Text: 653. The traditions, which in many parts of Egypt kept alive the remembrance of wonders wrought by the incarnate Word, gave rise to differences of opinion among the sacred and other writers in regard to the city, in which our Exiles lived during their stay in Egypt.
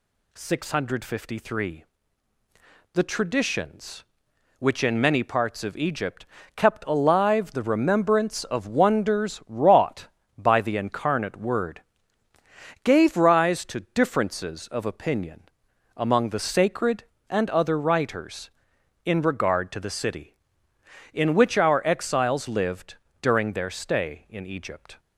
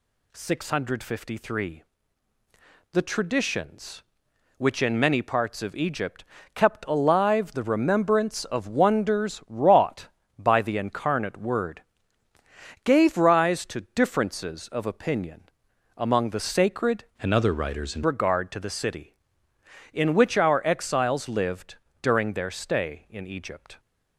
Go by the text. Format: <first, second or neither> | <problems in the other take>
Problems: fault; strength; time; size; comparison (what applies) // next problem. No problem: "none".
first | pauses between "Egypt" and "kept"; slight; at 6.2 s; 0.30 s long; slight in the first // pauses between "opinion" and "among"; noticeable; at 15.4 s; 0.54 s long; noticeable in the first // changes voice from "and" to "in"; from 17.2 to 18.0 s; 0.8 s long // pauses between "lived" and "during"; slight; at 21.7 s; 0.28 s long; slight in the first